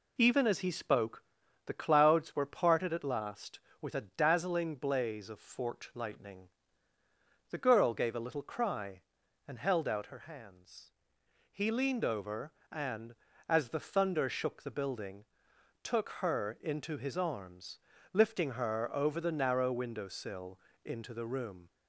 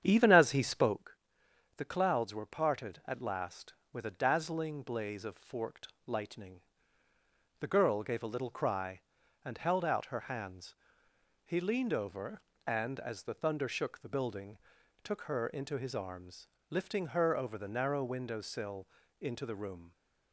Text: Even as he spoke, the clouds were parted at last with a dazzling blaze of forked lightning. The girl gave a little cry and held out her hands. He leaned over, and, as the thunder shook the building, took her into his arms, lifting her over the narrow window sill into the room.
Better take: first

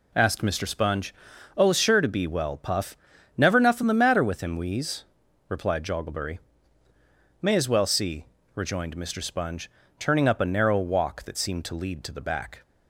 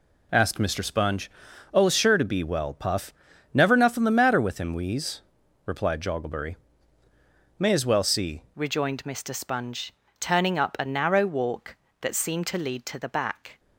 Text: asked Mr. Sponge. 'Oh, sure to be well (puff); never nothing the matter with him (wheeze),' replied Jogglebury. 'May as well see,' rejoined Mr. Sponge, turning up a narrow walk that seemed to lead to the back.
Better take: first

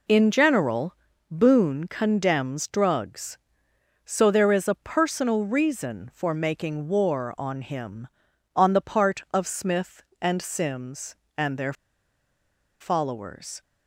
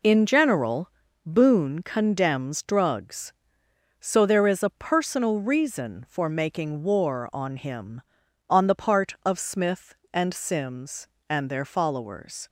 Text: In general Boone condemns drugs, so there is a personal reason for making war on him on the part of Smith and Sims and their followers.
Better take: second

